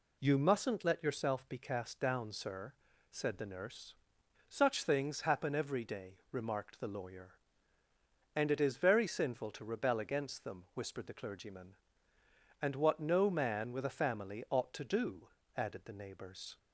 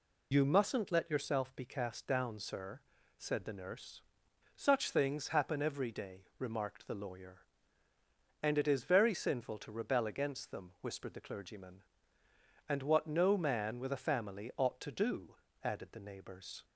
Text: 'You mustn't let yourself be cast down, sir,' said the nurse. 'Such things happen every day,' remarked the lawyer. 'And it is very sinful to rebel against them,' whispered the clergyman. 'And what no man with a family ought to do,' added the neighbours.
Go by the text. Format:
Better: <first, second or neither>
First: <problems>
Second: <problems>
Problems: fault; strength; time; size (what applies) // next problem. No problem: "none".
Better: first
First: none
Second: loses the start of "You"; at 0.3 s; 45 ms